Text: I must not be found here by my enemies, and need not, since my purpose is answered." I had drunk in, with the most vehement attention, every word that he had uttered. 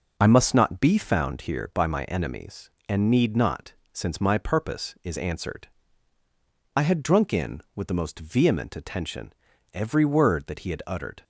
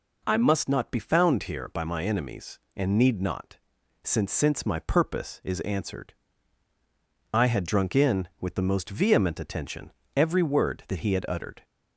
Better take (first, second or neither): first